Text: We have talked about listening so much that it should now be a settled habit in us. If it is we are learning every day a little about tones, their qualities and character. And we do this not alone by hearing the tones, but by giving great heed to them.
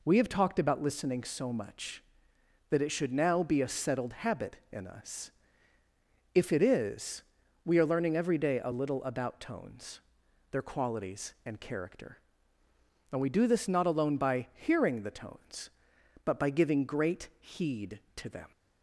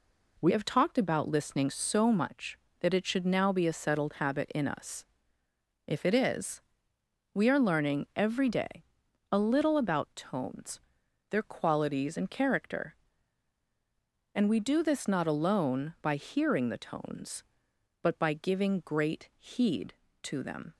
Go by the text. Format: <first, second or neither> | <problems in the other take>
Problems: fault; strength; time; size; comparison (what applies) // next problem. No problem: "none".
first | changes voice at "have"; from 0.4 s on; 20.3 s long // pauses between "is" and "we"; noticeable; at 6.6 s; 0.70 s long; also in the first // pauses between "day" and "a"; noticeable; at 8.8 s; 0.50 s long